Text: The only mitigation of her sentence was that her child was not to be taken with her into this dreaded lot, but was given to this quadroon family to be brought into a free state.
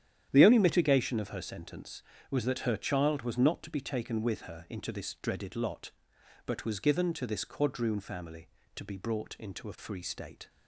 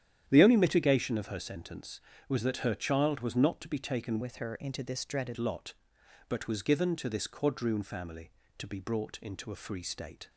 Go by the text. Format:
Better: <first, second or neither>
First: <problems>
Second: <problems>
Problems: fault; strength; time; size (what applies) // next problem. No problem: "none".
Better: first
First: starts louder than the rest; strong; until 1.3 s; 10 dB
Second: starts louder than the rest; strong; until 1.2 s; 10 dB // changes voice from "with" to "dreaded"; from 4.2 to 5.3 s; 1.1 s long